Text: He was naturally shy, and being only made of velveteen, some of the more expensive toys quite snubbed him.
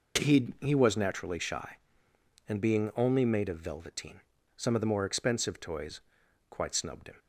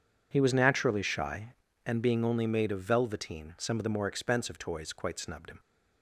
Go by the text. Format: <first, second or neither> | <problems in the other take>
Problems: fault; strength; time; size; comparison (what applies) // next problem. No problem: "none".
second | says "He" twice; at 0.6 s // pauses between "toys" and "quite"; noticeable; at 6.0 s; 0.48 s long